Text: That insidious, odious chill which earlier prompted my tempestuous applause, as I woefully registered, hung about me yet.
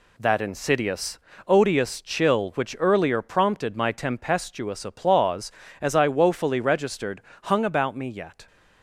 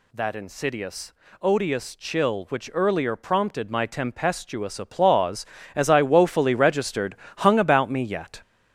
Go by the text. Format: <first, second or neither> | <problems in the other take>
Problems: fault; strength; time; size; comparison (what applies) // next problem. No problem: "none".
first | gets louder; throughout; 7 dB